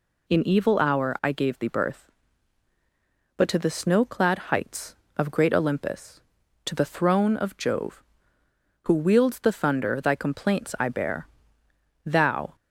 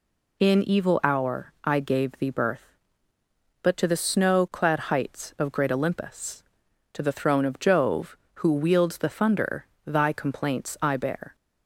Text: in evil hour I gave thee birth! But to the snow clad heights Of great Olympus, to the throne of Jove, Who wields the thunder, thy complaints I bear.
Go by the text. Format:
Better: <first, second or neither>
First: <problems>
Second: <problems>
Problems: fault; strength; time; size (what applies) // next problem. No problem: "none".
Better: second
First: goes on to say "Thou"; from 12.0 s on; 0.50 s long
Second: none